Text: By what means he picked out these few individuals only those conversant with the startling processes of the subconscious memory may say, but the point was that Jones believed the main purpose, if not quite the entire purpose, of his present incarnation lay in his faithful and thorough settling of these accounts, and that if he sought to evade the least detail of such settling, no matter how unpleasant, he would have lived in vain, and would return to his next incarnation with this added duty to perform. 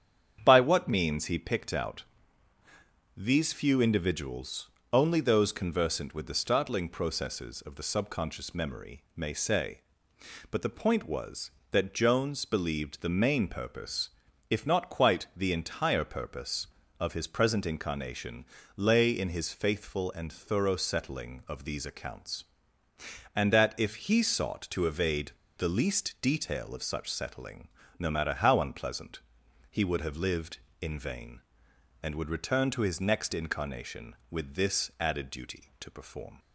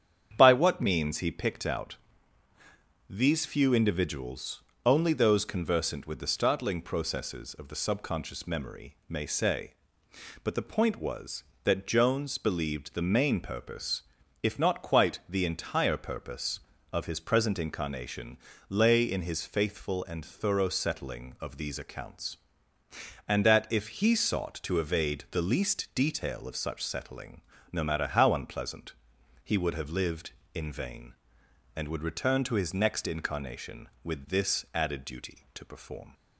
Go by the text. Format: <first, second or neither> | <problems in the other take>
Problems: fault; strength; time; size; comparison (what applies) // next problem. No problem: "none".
second | starts louder than the rest; strong; until 1.4 s; 8.5 dB; strong in the second // pauses between "out" and "these"; at 2.0 s; 1.1 s long; also in the second // pauses between "individuals" and "only"; slight; at 4.6 s; 0.22 s long; slight in the second // pauses between "incarnation" and "lay"; slight; at 18.4 s; 0.30 s long; slight in the second // pauses between "evade" and "the"; slight; at 25.3 s; 0.23 s long